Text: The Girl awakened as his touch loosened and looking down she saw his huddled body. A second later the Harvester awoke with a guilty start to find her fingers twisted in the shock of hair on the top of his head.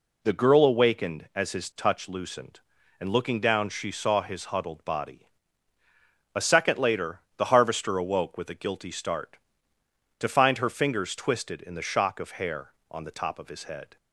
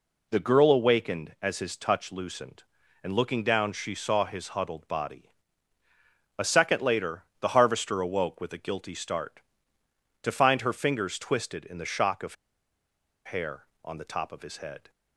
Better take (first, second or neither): first